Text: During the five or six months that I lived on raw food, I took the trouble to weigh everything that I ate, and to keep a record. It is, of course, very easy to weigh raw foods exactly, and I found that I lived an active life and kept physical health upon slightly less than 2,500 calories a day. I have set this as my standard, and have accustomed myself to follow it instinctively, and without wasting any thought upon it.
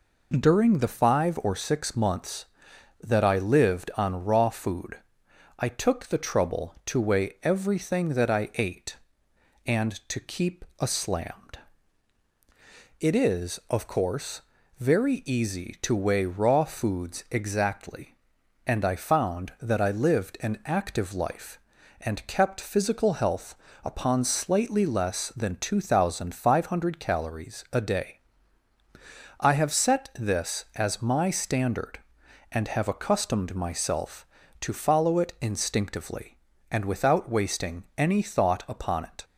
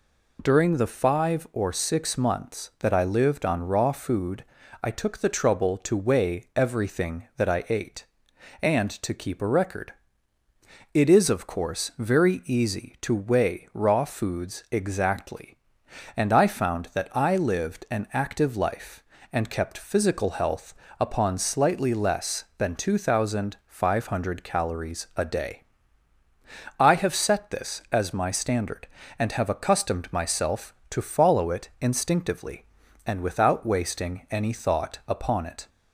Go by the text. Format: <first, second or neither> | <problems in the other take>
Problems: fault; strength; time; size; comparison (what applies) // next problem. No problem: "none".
second | pauses between "keep" and "a"; slight; at 10.6 s; 0.16 s long // says "slammed" for "record"; at 10.8 s // pauses between "health" and "upon"; slight; at 23.5 s; 0.30 s long; slight in the second // pauses between "wasting" and "any"; slight; at 37.8 s; 0.16 s long